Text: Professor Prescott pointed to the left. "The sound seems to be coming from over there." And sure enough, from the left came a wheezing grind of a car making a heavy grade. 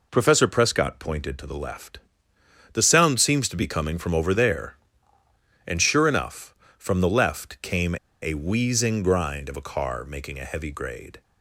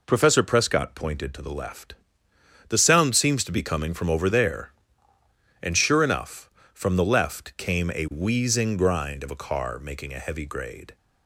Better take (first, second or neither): second